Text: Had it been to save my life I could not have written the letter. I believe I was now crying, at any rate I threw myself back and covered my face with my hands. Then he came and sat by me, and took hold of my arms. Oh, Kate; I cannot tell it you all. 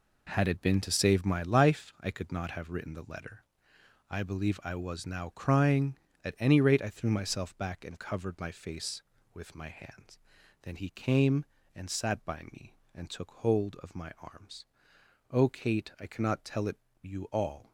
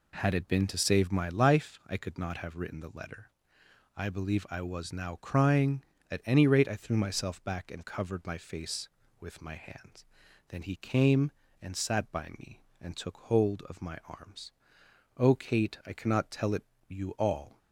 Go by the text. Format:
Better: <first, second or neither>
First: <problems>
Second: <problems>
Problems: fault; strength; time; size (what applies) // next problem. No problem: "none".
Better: second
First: gets quieter; strong; throughout; 9 dB // pauses between "it" and "you"; slight; at 16.7 s; 0.24 s long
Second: pauses between "it" and "you"; slight; at 16.6 s; 0.24 s long